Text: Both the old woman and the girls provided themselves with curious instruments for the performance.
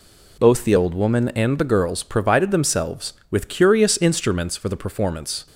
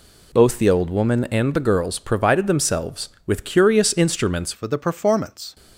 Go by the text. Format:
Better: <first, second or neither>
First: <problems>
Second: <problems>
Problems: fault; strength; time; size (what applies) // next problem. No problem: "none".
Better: first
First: none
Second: changes voice at "for"; from 4.5 s on; 1.0 s long